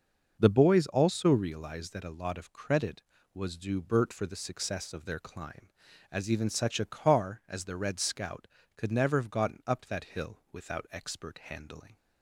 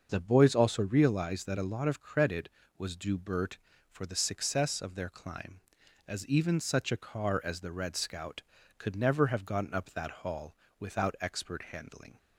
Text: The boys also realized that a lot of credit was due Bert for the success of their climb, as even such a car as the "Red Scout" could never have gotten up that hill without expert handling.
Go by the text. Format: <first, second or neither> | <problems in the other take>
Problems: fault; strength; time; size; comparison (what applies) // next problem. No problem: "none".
first | starts louder than the rest; until 1.1 s; 6.5 dB // says "hall" for "hill"; at 10.2 s